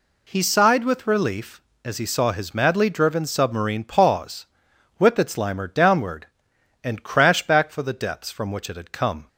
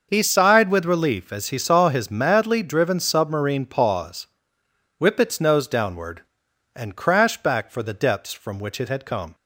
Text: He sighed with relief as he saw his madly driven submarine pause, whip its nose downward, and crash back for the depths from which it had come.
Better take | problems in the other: second | says "limer" for "nose"; at 5.3 s

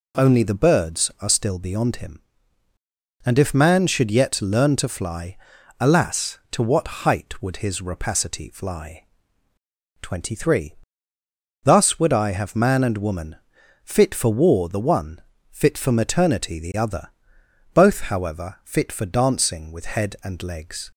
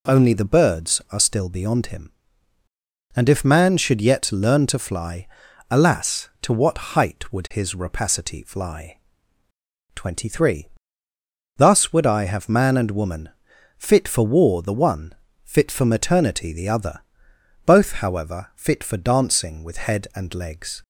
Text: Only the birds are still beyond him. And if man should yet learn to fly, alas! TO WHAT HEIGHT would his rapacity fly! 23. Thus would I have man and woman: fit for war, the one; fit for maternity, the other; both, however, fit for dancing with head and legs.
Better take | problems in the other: neither | pauses between "WHAT" and "HEIGHT"; slight; the same in both

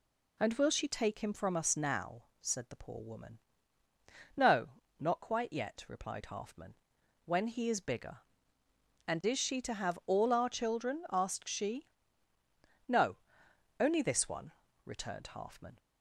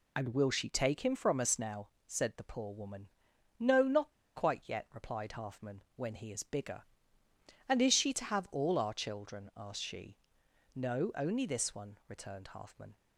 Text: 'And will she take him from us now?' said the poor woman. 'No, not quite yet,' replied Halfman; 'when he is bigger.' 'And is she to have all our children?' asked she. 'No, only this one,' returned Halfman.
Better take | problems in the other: first | pauses between "not" and "quite"; slight; at 4.1 s; 0.25 s long

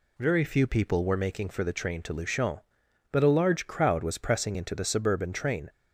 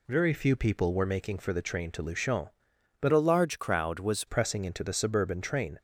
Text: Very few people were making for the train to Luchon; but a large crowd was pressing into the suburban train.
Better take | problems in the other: first | changes voice from "a" to "was"; from 3.0 to 4.2 s; 1.2 s long

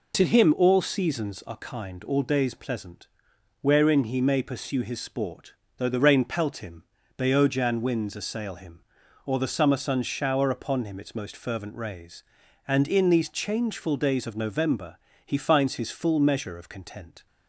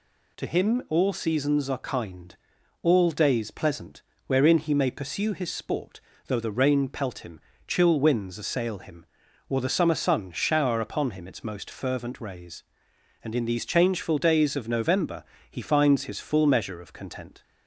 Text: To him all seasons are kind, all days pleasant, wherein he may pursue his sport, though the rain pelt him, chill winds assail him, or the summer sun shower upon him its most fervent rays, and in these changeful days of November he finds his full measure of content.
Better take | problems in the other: second | says "beojan" for "chill"; at 7.1 s // pauses between "November" and "he"; slight; at 14.9 s; 0.30 s long; slight in the second

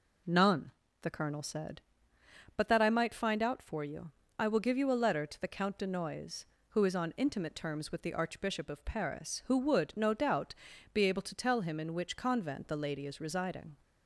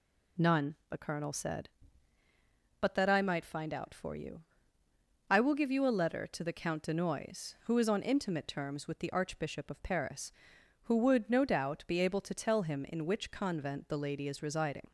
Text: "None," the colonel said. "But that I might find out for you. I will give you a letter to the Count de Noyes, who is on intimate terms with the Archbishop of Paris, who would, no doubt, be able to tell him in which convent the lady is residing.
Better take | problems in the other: neither | none

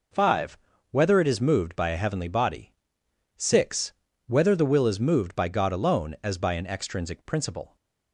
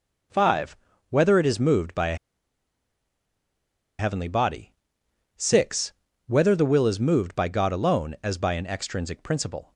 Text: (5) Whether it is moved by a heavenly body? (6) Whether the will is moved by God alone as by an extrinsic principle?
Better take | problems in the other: first | pauses between "a" and "heavenly"; strong; at 2.1 s; 1.8 s long

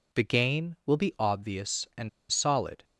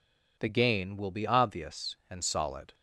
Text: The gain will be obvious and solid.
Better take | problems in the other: second | pauses between "and" and "solid"; slight; at 2.0 s; 0.21 s long

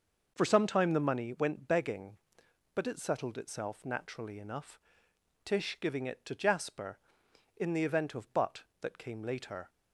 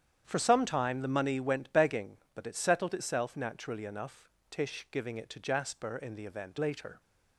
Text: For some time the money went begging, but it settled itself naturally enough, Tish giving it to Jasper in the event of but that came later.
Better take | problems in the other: first | starts louder than the rest; strong; until 1.2 s; 9 dB; noticeable in the first // skips "of but that came"; at 6.5 s

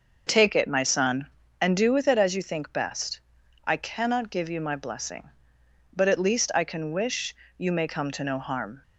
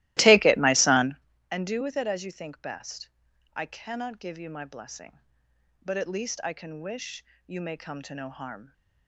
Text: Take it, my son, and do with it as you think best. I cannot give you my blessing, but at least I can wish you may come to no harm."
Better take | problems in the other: first | starts louder than the rest; strong; until 1.2 s; 17.5 dB // pauses between "wish" and "you"; slight; at 7.2 s; 0.22 s long; slight in the first

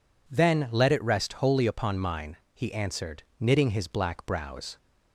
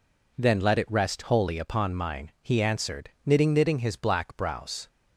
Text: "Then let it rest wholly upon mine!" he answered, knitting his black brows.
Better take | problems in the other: first | says "knitting" twice; at 3.5 s

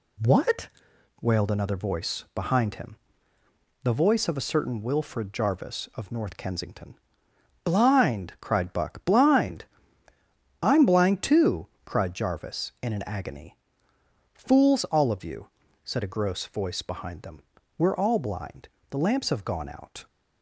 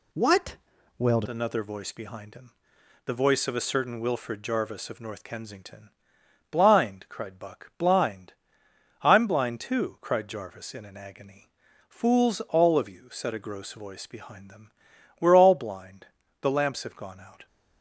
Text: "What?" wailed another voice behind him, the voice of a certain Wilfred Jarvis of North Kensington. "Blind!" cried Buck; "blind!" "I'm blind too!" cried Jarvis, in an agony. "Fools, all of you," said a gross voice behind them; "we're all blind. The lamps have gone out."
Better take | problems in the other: first | changes voice at "another"; from 1.2 s on; 16.2 s long

